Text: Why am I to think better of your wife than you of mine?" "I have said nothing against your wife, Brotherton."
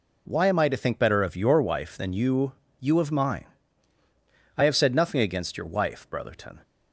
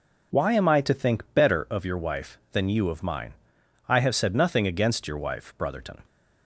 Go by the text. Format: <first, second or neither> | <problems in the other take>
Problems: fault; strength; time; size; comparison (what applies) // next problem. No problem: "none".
second | says "you" twice; at 2.8 s